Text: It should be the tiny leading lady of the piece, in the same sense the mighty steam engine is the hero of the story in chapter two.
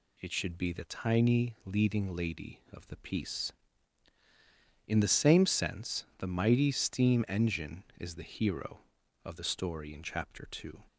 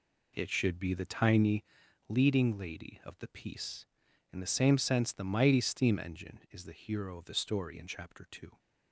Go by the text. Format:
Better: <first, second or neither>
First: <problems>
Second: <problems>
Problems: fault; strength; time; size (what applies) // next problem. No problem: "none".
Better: first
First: none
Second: starts louder than the rest; slight; until 1.6 s; 2.5 dB // pauses between "tiny" and "leading"; at 1.6 s; 0.44 s long